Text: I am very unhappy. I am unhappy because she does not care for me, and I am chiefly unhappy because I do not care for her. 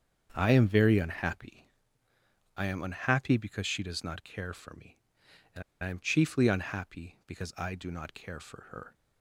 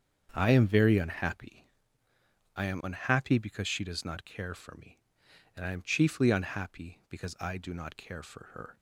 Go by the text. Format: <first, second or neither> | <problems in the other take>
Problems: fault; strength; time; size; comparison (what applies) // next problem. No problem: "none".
second | starts louder than the rest; strong; until 1.3 s; 7.5 dB; strong in the second // pauses between "and" and "I"; slight; at 5.6 s; 0.20 s long